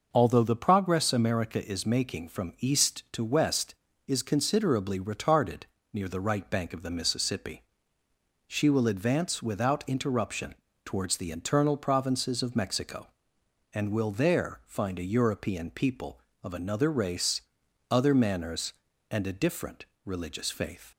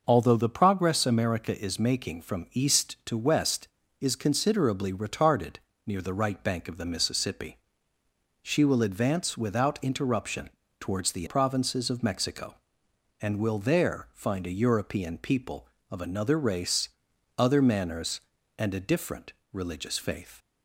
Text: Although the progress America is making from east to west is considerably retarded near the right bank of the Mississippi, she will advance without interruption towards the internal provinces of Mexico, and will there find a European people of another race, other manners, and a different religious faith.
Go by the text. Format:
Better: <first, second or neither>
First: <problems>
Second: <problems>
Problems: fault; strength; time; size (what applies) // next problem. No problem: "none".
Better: first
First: pauses between "retarded" and "near"; slight; at 5.6 s; 0.30 s long // pauses between "interruption" and "towards"; slight; at 10.5 s; 0.30 s long // pauses between "different" and "religious"; slight; at 19.8 s; 0.20 s long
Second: pauses between "retarded" and "near"; slight; at 5.5 s; 0.30 s long // pauses between "interruption" and "towards"; slight; at 10.5 s; 0.30 s long // skips "internal"; at 11.2 s // pauses between "different" and "religious"; slight; at 19.3 s; 0.20 s long